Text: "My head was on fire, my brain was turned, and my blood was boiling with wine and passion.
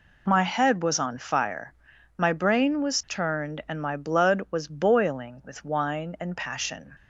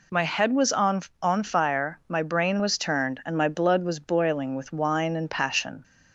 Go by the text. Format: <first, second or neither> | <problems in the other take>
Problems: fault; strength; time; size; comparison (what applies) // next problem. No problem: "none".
first | says "on" twice; at 1.1 s